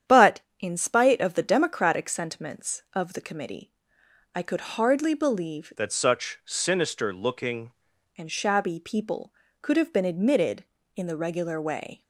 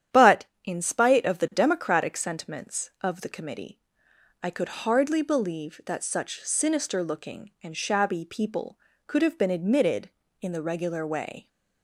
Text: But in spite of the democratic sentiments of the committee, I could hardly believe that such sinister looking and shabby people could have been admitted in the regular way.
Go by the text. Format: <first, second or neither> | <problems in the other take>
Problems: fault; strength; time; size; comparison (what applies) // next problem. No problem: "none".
second | starts louder than the rest; strong; until 1.2 s; 9 dB; strong in the second // changes voice from "that" to "looking"; from 5.7 to 7.7 s; 2.0 s long